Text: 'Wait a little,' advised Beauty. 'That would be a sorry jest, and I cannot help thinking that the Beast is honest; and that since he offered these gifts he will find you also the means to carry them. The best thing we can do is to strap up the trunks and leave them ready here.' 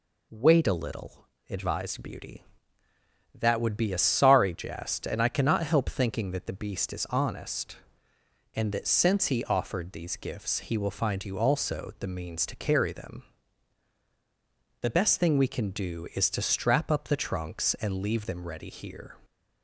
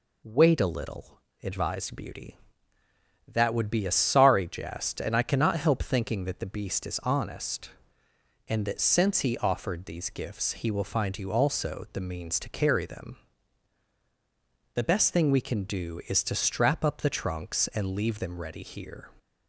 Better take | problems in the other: neither | none

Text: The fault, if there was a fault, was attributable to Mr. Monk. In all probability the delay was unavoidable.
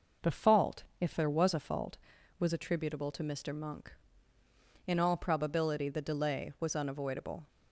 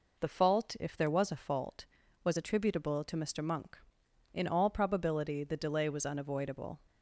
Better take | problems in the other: neither | none

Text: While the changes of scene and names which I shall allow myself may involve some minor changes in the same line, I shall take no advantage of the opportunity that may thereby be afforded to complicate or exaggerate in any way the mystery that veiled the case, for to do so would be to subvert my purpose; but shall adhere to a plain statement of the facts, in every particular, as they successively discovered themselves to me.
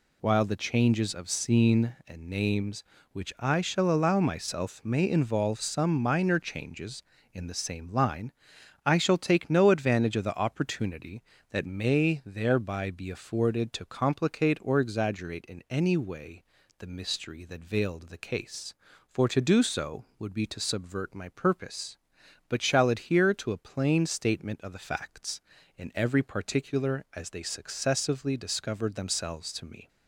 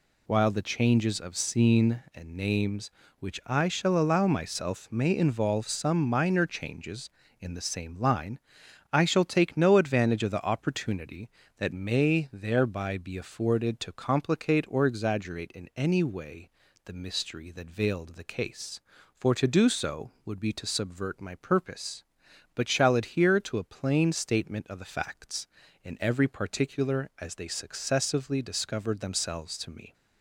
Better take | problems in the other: neither | pauses between "way" and "the"; slight; the same in both

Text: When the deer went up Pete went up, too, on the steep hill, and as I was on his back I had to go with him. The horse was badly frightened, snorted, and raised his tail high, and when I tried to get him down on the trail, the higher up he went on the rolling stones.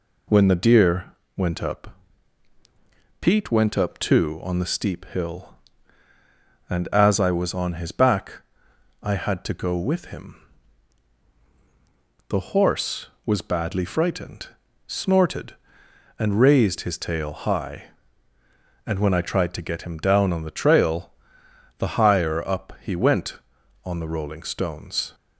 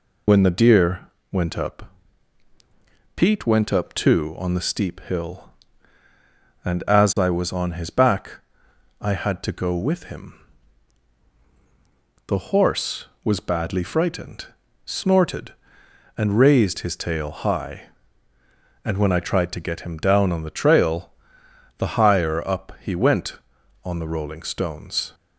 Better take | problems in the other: first | loses the start of "When"; at 0.2 s; 50 ms // pauses between "deer" and "went"; slight; at 1.0 s; 0.22 s long; slight in the first // pauses between "up" and "Pete"; at 1.9 s; 1.2 s long; also in the first // pauses between "back" and "I"; noticeable; at 8.4 s; 0.58 s long; noticeable in the first

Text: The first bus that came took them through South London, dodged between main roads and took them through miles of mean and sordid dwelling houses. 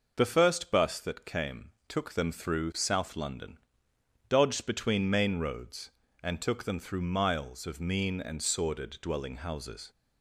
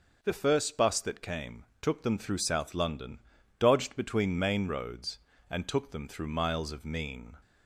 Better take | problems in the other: first | pauses between "came" and "took"; slight; at 1.6 s; 0.16 s long; slight in the first // stops before "and sordid dwelling houses"; at 7.4 s

